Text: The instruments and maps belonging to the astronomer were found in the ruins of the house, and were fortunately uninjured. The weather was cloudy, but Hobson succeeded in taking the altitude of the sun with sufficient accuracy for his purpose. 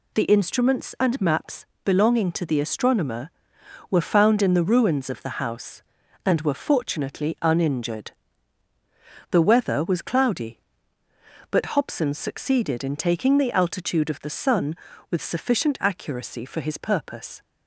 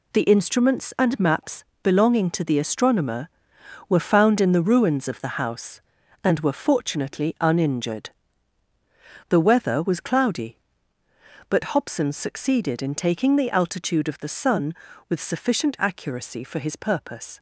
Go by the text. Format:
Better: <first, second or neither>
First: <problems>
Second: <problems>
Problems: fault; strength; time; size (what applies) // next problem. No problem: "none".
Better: first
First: pauses between "maps" and "belonging"; slight; at 1.6 s; 0.20 s long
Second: gets quieter; strong; throughout; 8 dB // pauses between "maps" and "belonging"; slight; at 1.6 s; 0.20 s long